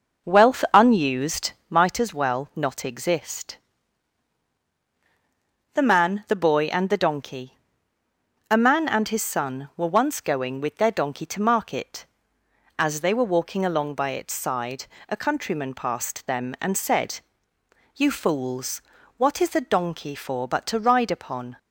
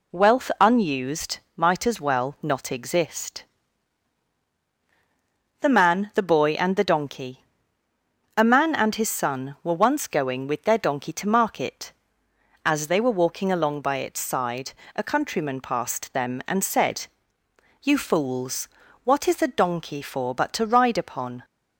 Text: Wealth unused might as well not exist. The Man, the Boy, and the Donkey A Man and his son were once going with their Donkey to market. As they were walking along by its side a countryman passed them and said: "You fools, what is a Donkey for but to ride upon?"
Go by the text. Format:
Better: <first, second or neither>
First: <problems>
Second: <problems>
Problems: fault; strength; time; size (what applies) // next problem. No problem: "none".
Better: second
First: starts louder than the rest; noticeable; until 2.0 s; 5.5 dB // pauses between "unused" and "might"; slight; at 1.5 s; 0.18 s long // pauses between "Donkey" and "A"; noticeable; at 7.5 s; 0.94 s long // pauses between "side" and "a"; slight; at 14.8 s; 0.24 s long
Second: pauses between "unused" and "might"; slight; at 1.3 s; 0.18 s long // pauses between "Donkey" and "A"; noticeable; at 7.4 s; 0.94 s long // pauses between "side" and "a"; slight; at 14.7 s; 0.24 s long